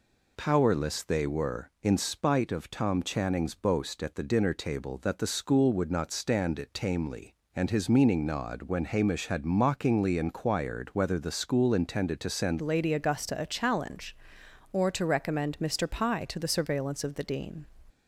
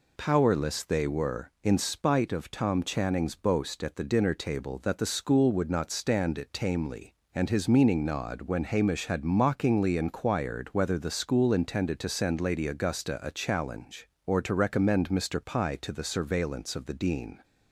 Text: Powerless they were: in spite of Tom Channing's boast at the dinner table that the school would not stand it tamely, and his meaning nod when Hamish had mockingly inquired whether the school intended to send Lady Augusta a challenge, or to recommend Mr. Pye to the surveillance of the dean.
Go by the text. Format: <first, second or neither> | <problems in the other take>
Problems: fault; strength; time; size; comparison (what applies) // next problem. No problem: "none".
second | changes voice at "Lady"; from 12.6 s on; 5.0 s long